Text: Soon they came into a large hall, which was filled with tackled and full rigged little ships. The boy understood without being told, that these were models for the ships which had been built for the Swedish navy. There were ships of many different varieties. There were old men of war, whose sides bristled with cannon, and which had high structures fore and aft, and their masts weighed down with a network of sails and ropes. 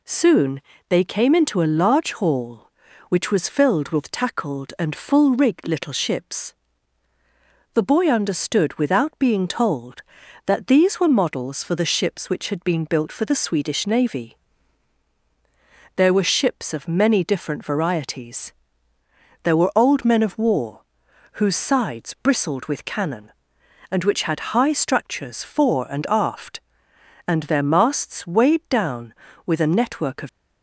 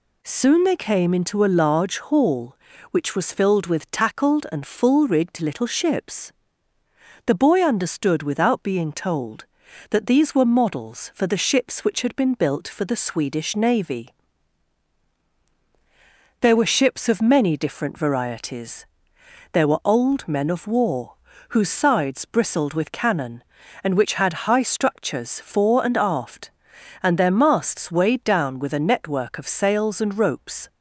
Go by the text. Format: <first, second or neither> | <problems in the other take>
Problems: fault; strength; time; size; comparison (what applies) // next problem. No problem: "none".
second | pauses between "Soon" and "they"; slight; at 0.6 s; 0.28 s long // stops before "sails and ropes"; at 30.2 s